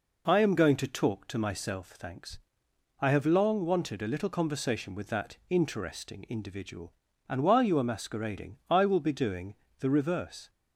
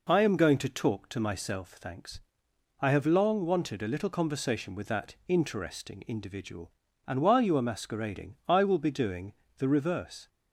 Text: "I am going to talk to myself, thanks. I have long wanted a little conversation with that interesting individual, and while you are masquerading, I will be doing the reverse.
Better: neither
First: pauses between "doing" and "the"; slight; at 9.5 s; 0.26 s long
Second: pauses between "doing" and "the"; slight; at 9.3 s; 0.26 s long

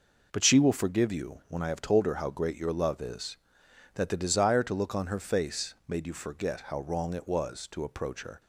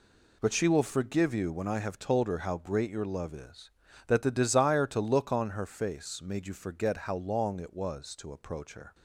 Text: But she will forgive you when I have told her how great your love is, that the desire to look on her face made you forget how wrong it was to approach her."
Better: first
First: none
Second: says "long" for "wrong"; at 7.1 s

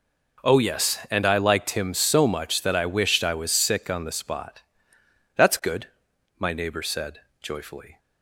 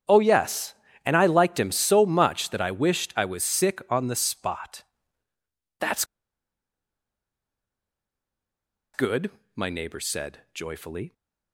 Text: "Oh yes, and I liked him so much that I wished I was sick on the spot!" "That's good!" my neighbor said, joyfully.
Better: first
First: none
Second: starts louder than the rest; strong; until 1.4 s; 8.5 dB // pauses between "That's" and "good"; strong; at 6.0 s; 2.9 s long

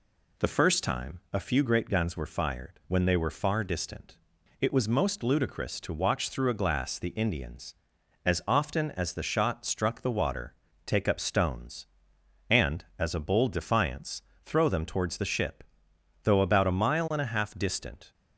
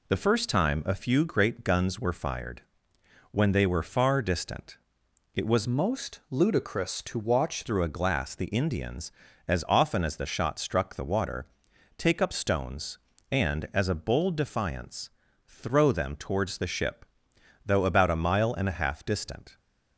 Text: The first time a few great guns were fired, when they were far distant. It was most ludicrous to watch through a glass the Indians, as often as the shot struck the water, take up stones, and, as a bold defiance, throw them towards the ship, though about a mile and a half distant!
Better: first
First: none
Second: changes voice from "most" to "watch"; from 5.6 to 7.6 s; 2.0 s long

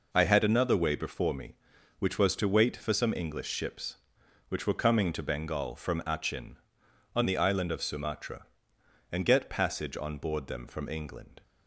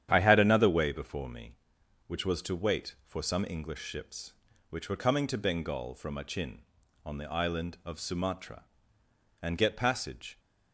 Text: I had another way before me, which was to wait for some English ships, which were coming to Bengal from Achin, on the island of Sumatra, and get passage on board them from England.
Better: first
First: none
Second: starts louder than the rest; strong; until 1.1 s; 9.5 dB // stops before "on board them from England"; at 10.3 s

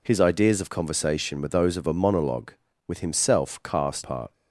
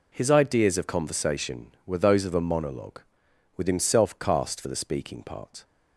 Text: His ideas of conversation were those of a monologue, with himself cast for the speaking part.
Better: second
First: skips "for the speaking"; at 4.0 s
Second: none

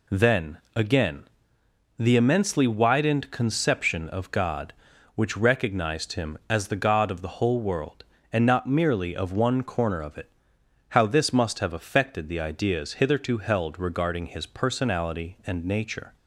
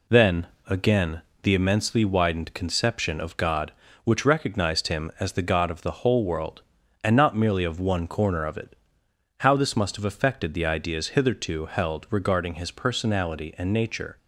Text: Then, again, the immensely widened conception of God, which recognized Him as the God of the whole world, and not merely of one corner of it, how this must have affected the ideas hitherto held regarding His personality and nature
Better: neither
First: none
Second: none

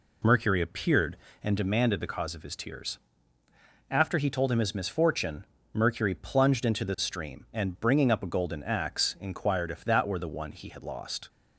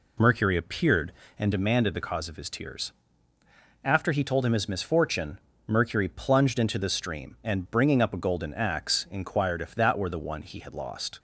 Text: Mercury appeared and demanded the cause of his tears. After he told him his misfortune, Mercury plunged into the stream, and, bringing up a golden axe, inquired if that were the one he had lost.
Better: neither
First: none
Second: none

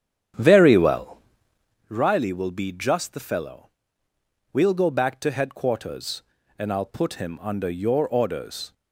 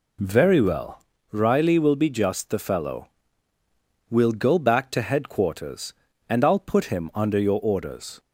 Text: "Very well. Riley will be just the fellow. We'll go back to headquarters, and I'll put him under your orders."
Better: second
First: starts louder than the rest; strong; until 1.9 s; 9 dB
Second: none

